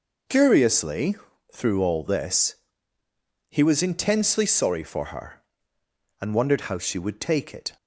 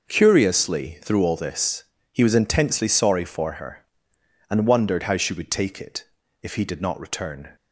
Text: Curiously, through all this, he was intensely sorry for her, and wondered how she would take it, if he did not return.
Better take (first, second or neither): second